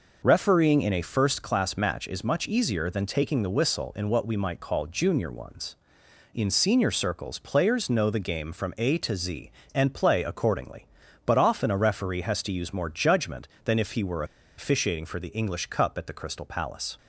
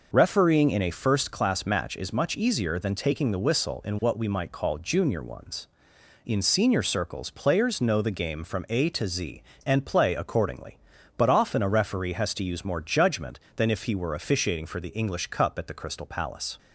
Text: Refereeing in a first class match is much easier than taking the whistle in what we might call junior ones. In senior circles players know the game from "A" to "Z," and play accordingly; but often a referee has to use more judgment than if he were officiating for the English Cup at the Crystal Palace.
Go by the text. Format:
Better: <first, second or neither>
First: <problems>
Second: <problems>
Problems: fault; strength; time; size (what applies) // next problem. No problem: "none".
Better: second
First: pauses between "were" and "officiating"; slight; at 14.2 s; 0.33 s long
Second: none